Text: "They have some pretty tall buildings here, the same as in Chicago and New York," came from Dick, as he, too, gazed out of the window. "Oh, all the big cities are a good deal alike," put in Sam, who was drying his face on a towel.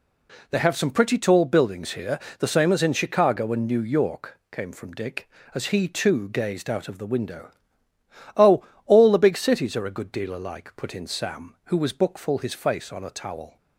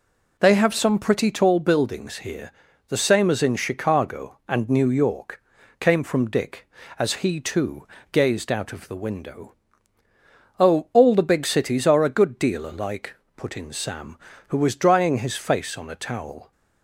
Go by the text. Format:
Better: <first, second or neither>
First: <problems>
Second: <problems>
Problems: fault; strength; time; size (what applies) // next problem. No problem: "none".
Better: second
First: says "bookful" for "drying"; at 11.9 s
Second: none